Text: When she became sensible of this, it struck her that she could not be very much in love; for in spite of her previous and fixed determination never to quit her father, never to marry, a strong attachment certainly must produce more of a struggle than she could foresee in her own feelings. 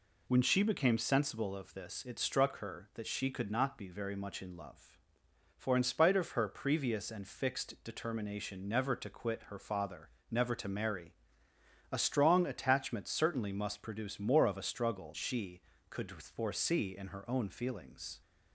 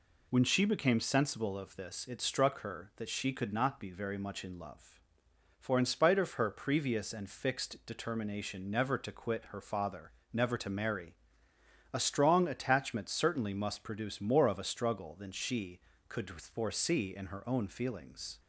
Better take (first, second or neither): second